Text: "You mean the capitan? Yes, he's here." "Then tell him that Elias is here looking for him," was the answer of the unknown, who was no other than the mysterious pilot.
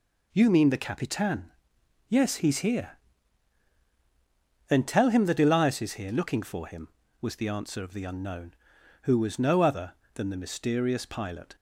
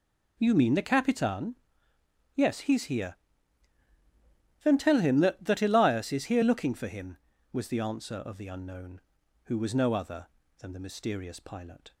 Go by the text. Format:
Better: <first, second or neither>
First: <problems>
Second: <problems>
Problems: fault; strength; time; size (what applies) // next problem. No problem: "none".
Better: first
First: none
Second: says "that" twice; at 5.4 s